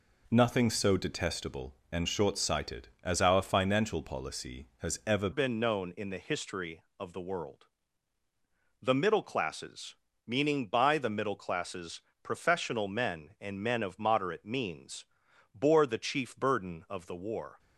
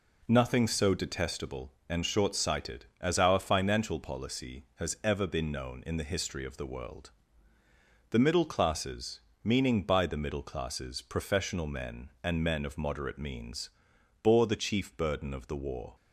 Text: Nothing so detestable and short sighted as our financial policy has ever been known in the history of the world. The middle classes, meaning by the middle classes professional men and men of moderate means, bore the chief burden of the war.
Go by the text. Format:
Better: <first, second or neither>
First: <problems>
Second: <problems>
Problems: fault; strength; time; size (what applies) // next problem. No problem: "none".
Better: second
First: changes voice at "been"; from 5.3 s on; 12.2 s long // pauses between "classes" and "professional"; slight; at 12.0 s; 0.22 s long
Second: none